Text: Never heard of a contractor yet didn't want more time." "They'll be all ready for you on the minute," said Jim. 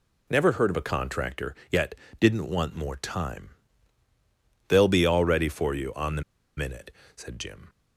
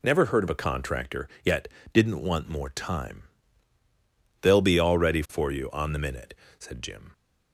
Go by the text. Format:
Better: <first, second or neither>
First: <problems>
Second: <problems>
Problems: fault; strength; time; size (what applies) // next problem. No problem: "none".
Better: second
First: pauses between "contractor" and "yet"; slight; at 1.5 s; 0.18 s long // pauses between "yet" and "didn't"; slight; at 1.9 s; 0.24 s long // pauses between "the" and "minute"; slight; at 6.2 s; 0.35 s long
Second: pauses between "contractor" and "yet"; slight; at 1.2 s; 0.18 s long // pauses between "yet" and "didn't"; slight; at 1.6 s; 0.24 s long